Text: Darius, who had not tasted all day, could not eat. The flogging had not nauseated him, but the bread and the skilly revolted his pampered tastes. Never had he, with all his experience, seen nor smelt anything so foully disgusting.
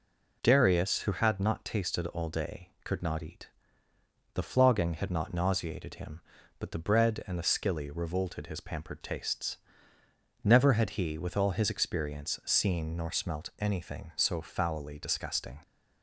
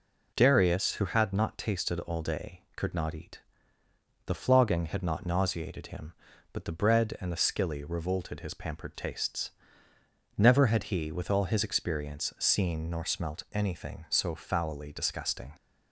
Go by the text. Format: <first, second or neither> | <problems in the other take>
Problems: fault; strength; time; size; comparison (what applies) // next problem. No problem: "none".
neither | none